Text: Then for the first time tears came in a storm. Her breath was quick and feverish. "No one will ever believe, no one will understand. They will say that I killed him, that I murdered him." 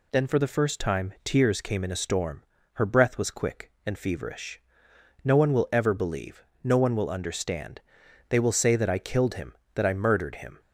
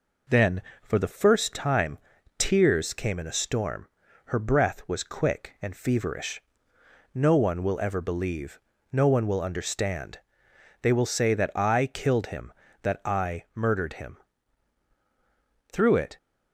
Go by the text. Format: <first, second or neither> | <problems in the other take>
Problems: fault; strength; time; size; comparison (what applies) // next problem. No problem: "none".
first | pauses between "time" and "tears"; at 1.9 s; 0.38 s long // goes on to say "Through it"; slight; from 15.7 s on; 0.46 s long